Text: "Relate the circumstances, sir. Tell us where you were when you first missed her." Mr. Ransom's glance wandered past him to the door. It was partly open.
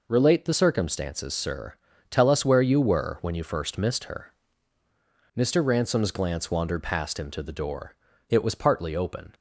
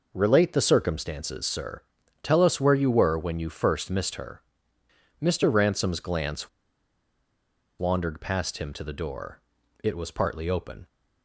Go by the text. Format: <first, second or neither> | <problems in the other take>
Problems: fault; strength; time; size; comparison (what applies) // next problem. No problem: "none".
first | pauses between "glance" and "wandered"; strong; at 6.4 s; 1.3 s long